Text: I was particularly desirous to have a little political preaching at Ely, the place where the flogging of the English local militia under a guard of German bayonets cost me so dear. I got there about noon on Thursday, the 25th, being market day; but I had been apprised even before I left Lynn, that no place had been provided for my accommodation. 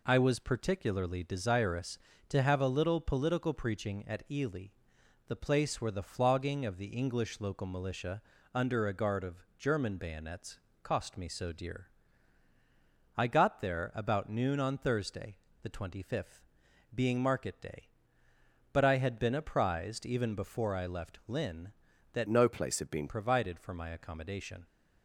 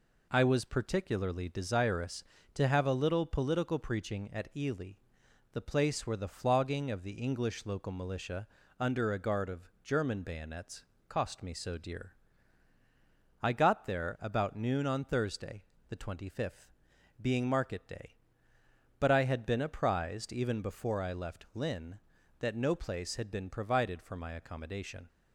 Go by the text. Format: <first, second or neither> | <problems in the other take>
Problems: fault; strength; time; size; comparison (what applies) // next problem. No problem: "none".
second | pauses between "militia" and "under"; slight; at 8.2 s; 0.32 s long; slight in the second // pauses between "bayonets" and "cost"; slight; at 10.5 s; 0.24 s long; slight in the second // changes voice from "no" to "been"; from 22.2 to 23.0 s; 0.8 s long